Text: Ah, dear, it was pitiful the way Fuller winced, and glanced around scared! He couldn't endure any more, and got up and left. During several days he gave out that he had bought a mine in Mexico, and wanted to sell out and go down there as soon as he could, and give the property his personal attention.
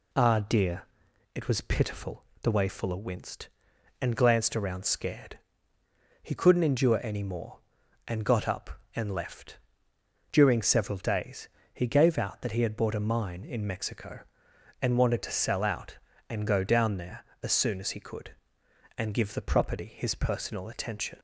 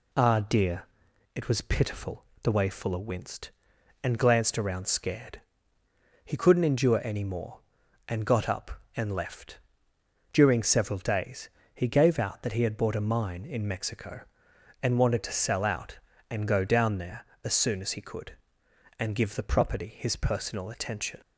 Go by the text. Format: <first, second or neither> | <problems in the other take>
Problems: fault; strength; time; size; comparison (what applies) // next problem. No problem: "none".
neither | pauses between "pitiful" and "the"; slight; the same in both // pauses between "days" and "he"; slight; the same in both